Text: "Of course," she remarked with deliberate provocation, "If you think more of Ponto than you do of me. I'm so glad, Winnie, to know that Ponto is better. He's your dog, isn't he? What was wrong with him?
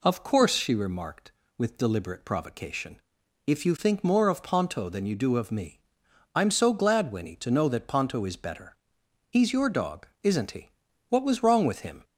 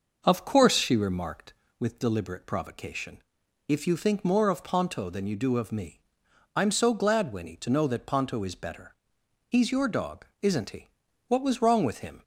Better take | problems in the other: first | starts louder than the rest; noticeable; until 1.8 s; 6 dB

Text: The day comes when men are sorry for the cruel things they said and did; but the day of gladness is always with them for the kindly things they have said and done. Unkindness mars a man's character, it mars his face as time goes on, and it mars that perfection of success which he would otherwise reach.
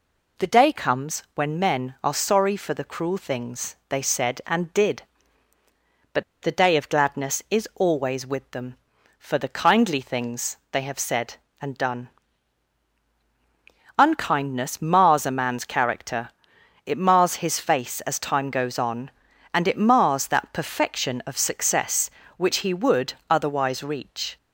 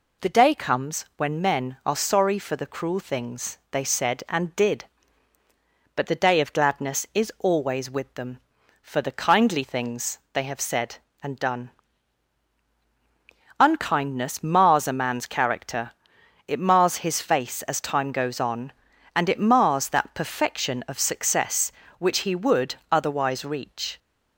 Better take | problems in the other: second | pauses between "but" and "the"; slight; at 6.2 s; 0.18 s long // pauses between "things" and "they"; slight; at 10.5 s; 0.16 s long; slight in the second

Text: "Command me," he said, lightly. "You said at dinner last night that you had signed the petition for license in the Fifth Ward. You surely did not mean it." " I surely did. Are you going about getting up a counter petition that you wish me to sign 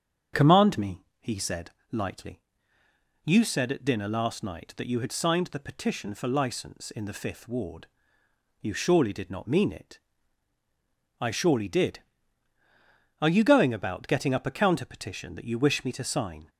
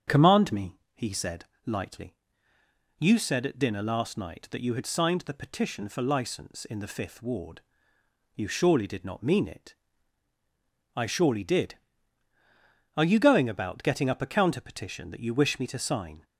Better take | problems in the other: neither | starts louder than the rest; strong; the same in both

